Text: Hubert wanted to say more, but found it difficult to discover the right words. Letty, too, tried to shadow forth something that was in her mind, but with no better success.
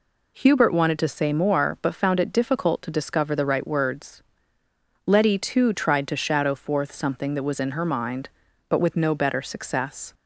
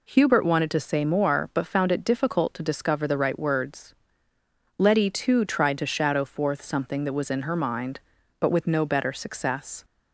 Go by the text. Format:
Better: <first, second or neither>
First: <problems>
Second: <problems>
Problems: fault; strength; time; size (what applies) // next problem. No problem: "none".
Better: neither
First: none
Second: none